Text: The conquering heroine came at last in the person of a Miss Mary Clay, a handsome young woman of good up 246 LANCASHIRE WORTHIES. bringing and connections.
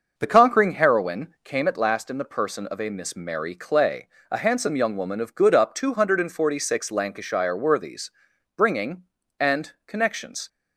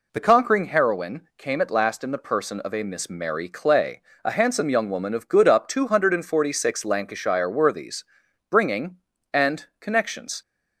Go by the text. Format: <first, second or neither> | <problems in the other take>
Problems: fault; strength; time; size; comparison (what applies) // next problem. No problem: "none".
second | starts louder than the rest; until 1.8 s; 6 dB